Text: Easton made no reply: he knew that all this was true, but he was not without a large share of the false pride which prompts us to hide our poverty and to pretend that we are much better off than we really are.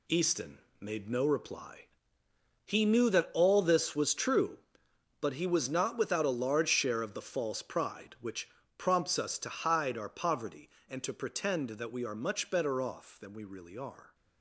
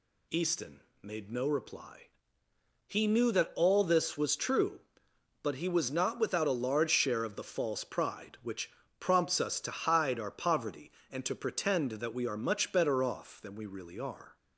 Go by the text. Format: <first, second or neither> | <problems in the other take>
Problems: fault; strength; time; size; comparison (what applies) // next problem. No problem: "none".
second | gets quieter; strong; throughout; 8.5 dB // pauses between "Easton" and "made"; slight; at 0.5 s; 0.20 s long; slight in the second // pauses between "which" and "prompts"; slight; at 8.4 s; 0.28 s long; slight in the second